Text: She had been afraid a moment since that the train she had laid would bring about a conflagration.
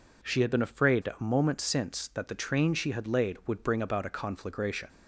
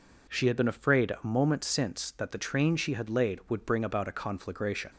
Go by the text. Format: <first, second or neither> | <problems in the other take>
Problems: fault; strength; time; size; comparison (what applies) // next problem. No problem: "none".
neither | none